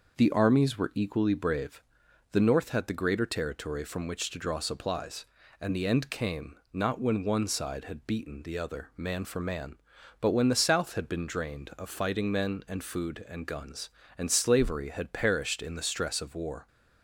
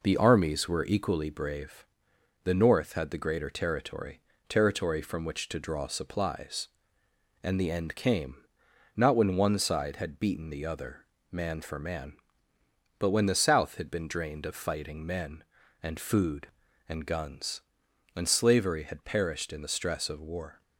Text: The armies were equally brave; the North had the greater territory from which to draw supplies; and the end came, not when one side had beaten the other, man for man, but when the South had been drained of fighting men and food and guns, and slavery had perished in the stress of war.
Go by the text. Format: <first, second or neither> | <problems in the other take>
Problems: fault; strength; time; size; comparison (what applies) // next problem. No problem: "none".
first | says "territory" twice; at 4.4 s